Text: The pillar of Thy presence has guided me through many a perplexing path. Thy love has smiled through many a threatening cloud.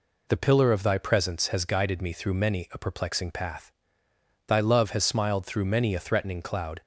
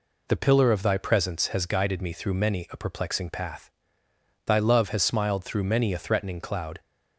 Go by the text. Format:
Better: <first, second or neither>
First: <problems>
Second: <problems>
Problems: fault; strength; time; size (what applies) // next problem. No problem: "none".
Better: neither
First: none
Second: none